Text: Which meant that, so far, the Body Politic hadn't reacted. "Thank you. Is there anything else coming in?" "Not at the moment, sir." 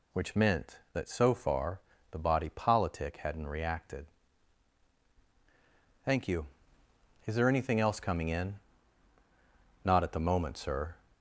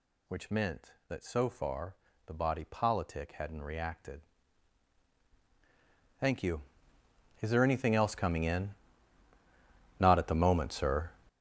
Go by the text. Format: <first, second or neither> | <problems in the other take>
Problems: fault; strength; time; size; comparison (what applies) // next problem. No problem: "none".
first | gets louder; strong; throughout; 12.5 dB